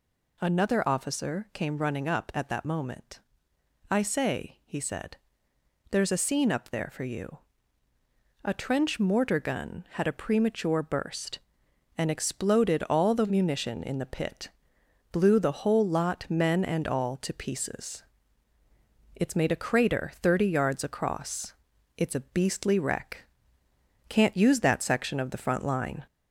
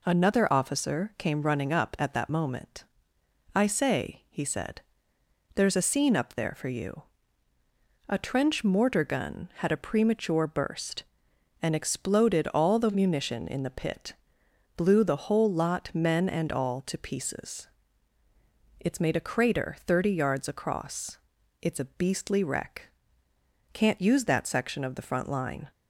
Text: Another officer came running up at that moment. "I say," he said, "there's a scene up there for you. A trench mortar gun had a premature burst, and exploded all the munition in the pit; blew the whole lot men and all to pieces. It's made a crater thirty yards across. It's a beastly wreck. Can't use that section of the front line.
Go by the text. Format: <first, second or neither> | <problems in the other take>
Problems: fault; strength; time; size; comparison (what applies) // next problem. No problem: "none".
second | gets louder; slight; throughout; 2 dB